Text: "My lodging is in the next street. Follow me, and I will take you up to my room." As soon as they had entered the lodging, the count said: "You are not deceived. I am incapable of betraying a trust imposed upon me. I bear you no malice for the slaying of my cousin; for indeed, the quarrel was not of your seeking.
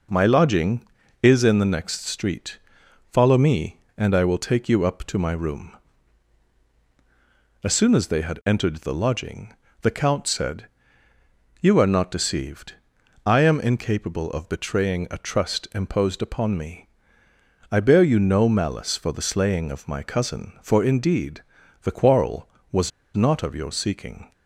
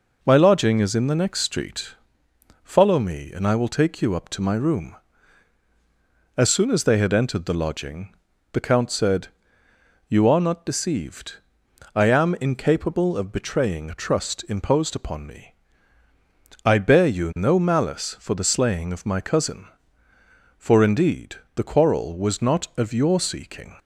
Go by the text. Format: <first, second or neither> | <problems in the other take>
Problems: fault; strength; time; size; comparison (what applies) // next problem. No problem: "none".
second | pauses between "was" and "not"; slight; at 22.9 s; 0.25 s long